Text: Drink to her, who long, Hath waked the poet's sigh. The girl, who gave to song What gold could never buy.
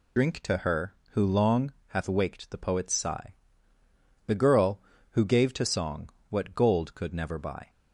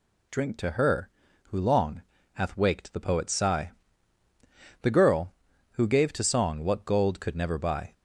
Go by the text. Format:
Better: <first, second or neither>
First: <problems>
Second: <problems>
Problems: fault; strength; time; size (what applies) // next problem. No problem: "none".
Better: second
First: loses the start of "Drink"; at 0.1 s; 45 ms // pauses between "song" and "What"; slight; at 6.0 s; 0.20 s long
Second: none